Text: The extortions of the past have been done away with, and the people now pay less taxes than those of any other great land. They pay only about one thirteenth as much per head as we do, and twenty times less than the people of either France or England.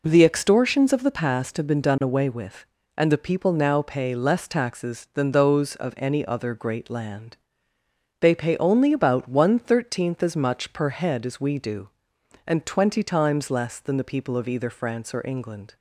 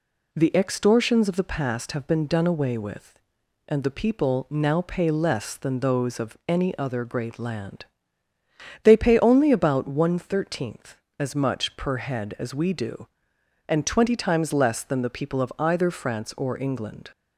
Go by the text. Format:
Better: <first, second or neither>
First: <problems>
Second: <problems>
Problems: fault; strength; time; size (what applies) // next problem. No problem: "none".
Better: first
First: none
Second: skips "taxes"; at 5.5 s